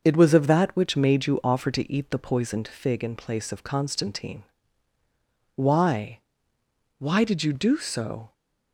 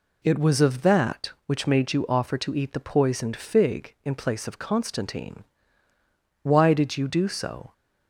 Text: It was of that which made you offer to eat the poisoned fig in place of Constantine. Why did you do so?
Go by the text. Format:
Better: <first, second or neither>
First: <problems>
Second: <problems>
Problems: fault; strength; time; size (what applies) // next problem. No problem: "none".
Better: second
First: starts louder than the rest; noticeable; until 1.0 s; 6 dB // says "Why" twice; at 6.9 s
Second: none